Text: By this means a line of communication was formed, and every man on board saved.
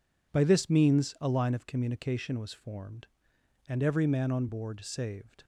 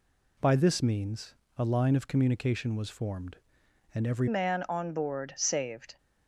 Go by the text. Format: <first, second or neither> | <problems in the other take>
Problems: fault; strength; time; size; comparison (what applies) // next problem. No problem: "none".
first | pauses between "means" and "a"; slight; at 1.3 s; 0.24 s long // changes voice at "man"; from 4.2 s on; 1.7 s long